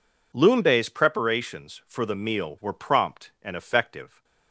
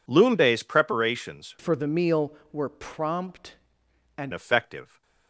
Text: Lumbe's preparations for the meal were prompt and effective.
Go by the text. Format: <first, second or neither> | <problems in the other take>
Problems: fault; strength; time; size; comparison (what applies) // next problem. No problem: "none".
first | changes voice from "for" to "and"; from 1.5 to 4.3 s; 2.8 s long